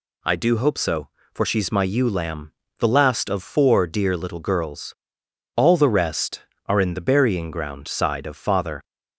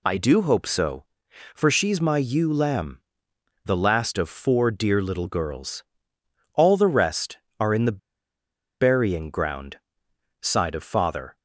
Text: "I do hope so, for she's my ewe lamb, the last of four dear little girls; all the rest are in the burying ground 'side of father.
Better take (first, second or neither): first